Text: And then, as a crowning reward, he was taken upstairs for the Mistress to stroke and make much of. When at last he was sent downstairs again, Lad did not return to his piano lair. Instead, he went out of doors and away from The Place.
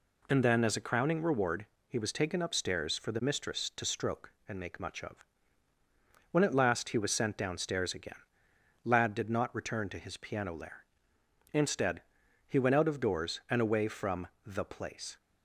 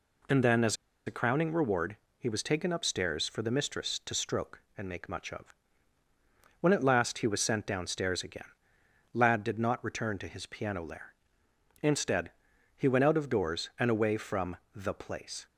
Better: first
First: pauses between "from" and "The"; slight; at 14.2 s; 0.18 s long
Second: pauses between "as" and "a"; slight; at 0.7 s; 0.31 s long // pauses between "from" and "The"; slight; at 14.5 s; 0.18 s long

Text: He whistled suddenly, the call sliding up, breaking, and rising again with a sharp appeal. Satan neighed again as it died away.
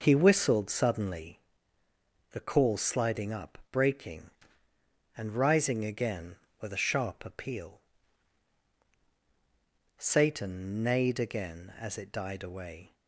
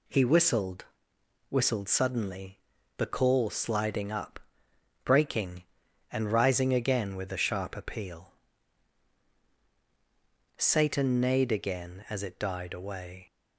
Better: first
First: none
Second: says "whistled" twice; at 1.4 s

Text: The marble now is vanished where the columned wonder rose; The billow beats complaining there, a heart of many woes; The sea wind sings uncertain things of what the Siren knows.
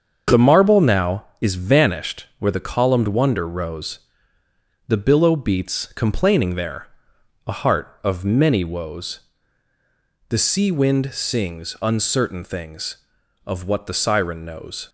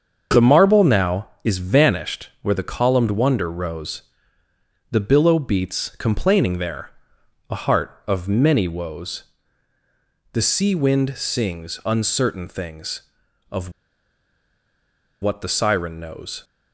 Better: first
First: starts louder than the rest; until 1.4 s; 7 dB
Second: starts louder than the rest; until 1.4 s; 7 dB // pauses between "of" and "what"; strong; at 13.7 s; 1.5 s long

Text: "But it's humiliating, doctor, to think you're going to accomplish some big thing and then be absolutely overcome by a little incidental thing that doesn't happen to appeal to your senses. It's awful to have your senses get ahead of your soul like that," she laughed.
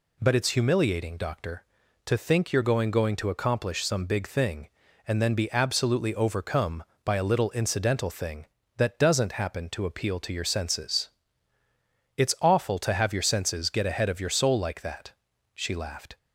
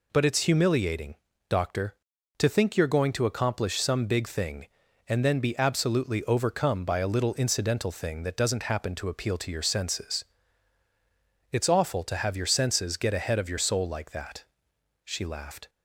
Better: second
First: says "going" twice; at 2.9 s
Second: none

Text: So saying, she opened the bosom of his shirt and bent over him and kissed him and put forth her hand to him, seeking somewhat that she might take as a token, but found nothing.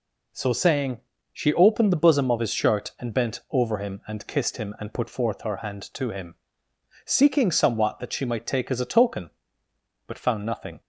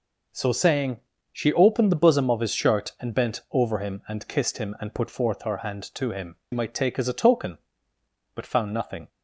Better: first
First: none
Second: skips "seeking somewhat that she"; at 6.4 s

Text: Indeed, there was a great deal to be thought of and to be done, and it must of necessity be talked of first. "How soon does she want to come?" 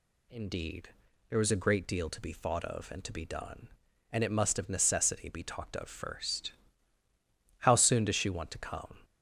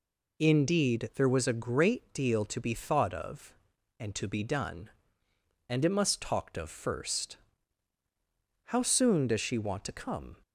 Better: first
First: none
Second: skips "of necessity be"; at 6.2 s

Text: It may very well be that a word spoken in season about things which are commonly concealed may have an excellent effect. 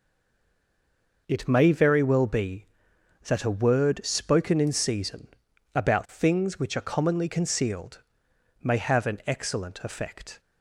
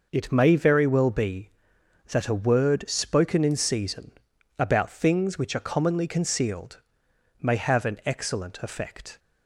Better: second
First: stays silent before the first word; noticeable; until 1.2 s; 1.2 s long // pauses between "season" and "about"; noticeable; at 5.2 s; 0.46 s long // pauses between "concealed" and "may"; noticeable; at 8.0 s; 0.60 s long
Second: pauses between "season" and "about"; noticeable; at 4.1 s; 0.46 s long // pauses between "concealed" and "may"; noticeable; at 6.8 s; 0.60 s long

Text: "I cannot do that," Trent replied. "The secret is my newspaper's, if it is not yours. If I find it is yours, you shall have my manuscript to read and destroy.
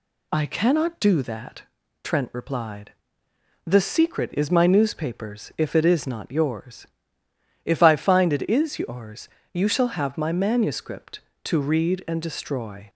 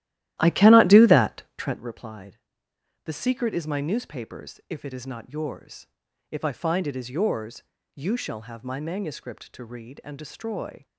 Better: first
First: none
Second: starts louder than the rest; strong; until 1.8 s; 14 dB

